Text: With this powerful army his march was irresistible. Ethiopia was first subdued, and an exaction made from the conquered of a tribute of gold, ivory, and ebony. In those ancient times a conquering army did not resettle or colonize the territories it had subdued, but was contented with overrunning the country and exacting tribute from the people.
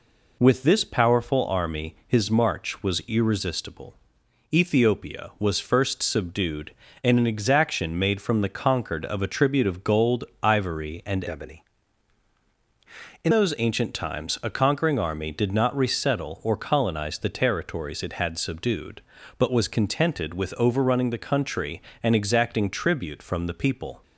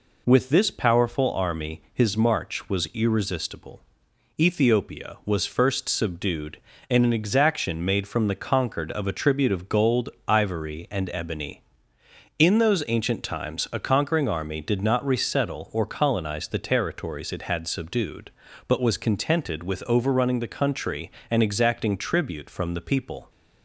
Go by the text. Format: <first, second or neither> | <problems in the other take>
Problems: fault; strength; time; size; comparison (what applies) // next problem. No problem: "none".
second | changes voice from "ebony" to "In"; from 11.2 to 13.3 s; 2.1 s long